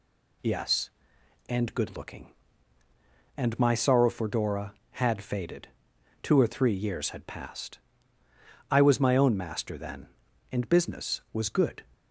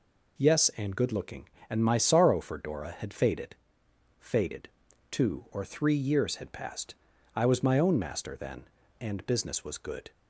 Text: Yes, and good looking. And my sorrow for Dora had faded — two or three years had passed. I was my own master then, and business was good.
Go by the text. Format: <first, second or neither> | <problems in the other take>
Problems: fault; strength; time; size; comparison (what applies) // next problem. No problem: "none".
first | says "faded" twice; at 4.1 s